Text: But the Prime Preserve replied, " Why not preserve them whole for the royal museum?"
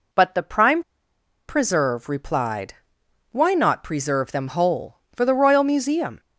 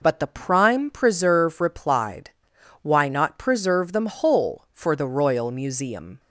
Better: second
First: pauses between "Prime" and "Preserve"; noticeable; at 0.8 s; 0.66 s long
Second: none

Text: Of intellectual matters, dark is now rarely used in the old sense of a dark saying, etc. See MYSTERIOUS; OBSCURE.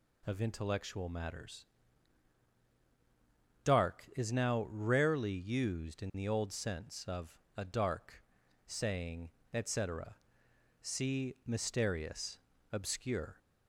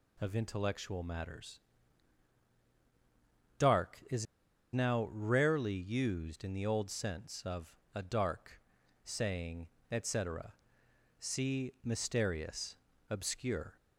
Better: first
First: pauses between "of" and "a"; slight; at 7.3 s; 0.18 s long // pauses between "dark" and "saying"; at 8.2 s; 0.44 s long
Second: pauses between "is" and "now"; noticeable; at 4.2 s; 0.48 s long // pauses between "of" and "a"; slight; at 7.7 s; 0.18 s long // pauses between "dark" and "saying"; at 8.5 s; 0.44 s long

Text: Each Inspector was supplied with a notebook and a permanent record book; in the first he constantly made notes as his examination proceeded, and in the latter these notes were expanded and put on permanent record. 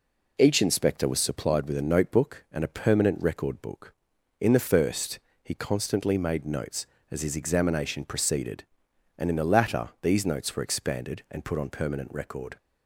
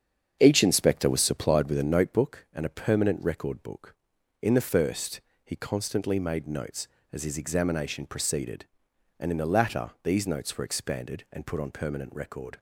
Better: first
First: pauses between "first" and "he"; slight; at 5.1 s; 0.24 s long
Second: starts louder than the rest; strong; until 2.1 s; 8 dB // pauses between "first" and "he"; slight; at 5.2 s; 0.24 s long

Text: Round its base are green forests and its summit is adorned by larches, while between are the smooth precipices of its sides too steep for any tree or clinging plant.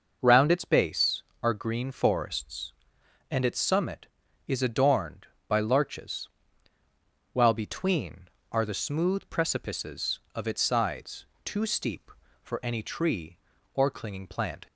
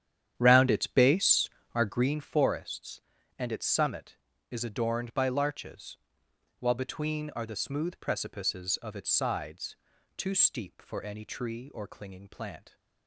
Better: first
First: pauses between "sides" and "too"; slight; at 11.2 s; 0.20 s long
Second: starts louder than the rest; strong; until 2.1 s; 9.5 dB // pauses between "sides" and "too"; at 9.7 s; 0.42 s long

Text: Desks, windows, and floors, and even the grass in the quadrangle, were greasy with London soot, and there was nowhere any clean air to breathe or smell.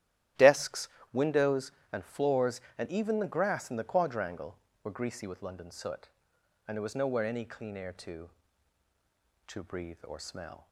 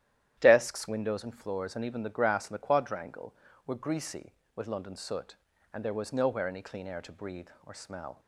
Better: second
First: starts louder than the rest; strong; until 1.6 s; 12.5 dB // says "to" twice; at 9.4 s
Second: starts louder than the rest; strong; until 1.4 s; 11.5 dB

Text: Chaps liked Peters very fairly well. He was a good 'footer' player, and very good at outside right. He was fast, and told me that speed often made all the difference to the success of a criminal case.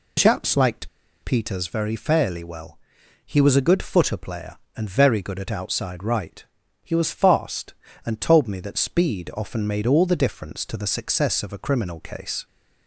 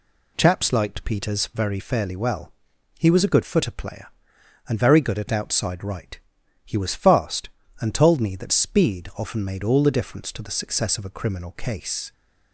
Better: second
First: pauses between "liked" and "Peters"; slight; at 0.8 s; 0.34 s long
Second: none

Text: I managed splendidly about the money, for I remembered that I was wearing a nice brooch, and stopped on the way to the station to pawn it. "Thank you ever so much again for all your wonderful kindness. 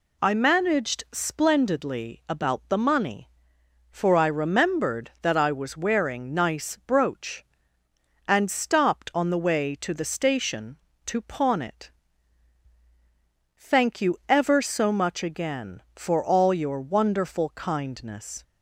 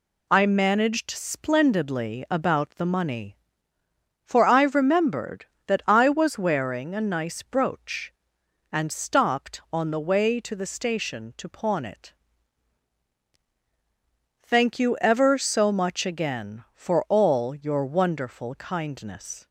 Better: second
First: skips "a"; at 6.3 s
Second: none

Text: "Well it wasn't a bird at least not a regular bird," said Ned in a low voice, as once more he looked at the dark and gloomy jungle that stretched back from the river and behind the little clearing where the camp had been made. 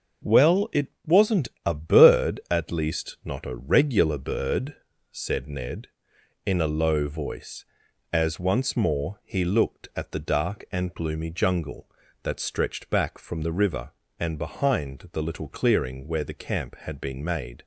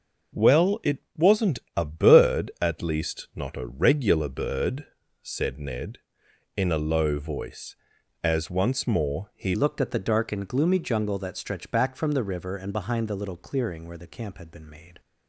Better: first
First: starts louder than the rest; until 1.4 s; 6.5 dB // pauses between "it" and "wasn't"; slight; at 0.8 s; 0.18 s long // pauses between "wasn't" and "a"; slight; at 1.4 s; 0.16 s long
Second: starts louder than the rest; until 1.5 s; 6 dB // pauses between "it" and "wasn't"; slight; at 0.9 s; 0.18 s long // pauses between "wasn't" and "a"; slight; at 1.5 s; 0.16 s long // changes voice at "looked"; from 9.5 s on; 5.5 s long

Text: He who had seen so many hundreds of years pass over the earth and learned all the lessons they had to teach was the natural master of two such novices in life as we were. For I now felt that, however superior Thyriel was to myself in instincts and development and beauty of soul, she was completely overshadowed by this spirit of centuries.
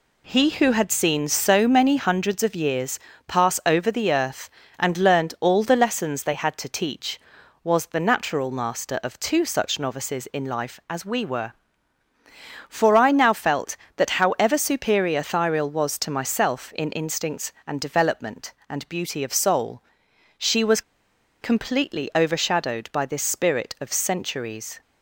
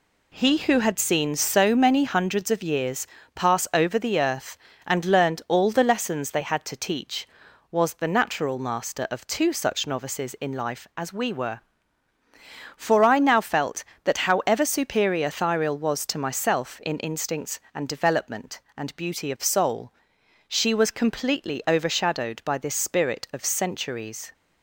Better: second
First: pauses between "years" and "pass"; slight; at 2.9 s; 0.30 s long // pauses between "was" and "completely"; noticeable; at 20.8 s; 0.60 s long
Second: pauses between "years" and "pass"; slight; at 3.0 s; 0.30 s long

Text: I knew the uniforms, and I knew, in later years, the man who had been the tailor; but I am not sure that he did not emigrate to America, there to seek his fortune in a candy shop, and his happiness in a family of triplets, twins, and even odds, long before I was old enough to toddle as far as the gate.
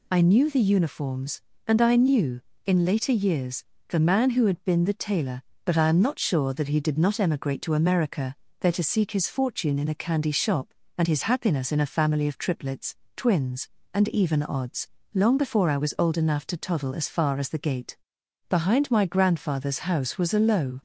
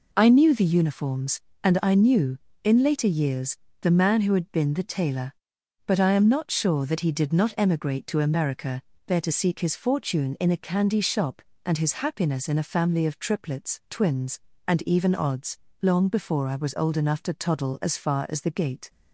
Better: second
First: goes on to say "Behind my grandfather's house was a low"; strong; from 18.4 s on; 2.3 s long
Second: none

